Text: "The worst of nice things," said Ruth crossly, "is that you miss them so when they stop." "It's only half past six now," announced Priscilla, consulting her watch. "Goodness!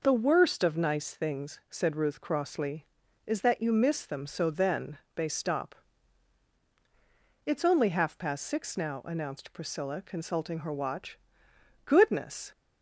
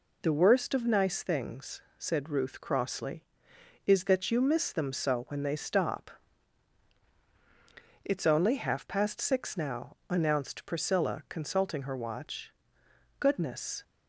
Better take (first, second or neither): second